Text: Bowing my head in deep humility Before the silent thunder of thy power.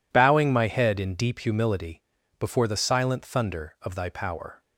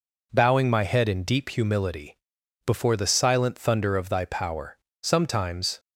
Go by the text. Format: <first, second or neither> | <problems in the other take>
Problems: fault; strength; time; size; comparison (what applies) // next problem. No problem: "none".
first | pauses between "humility" and "Before"; noticeable; at 2.1 s; 0.52 s long; also in the first // goes on to say "Sometimes"; noticeable; from 5.0 s on; 0.78 s long